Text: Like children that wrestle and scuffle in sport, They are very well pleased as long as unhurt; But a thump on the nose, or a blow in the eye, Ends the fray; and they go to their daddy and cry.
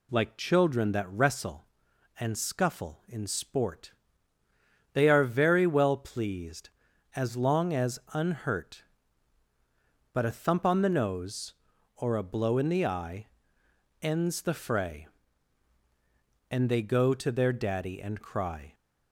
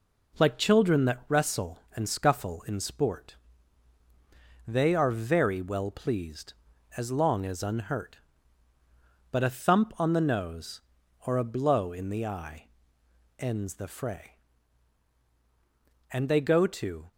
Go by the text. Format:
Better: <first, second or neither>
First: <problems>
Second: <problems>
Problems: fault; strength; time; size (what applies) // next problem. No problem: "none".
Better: first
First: none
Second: stops before "their daddy and cry"; at 17.1 s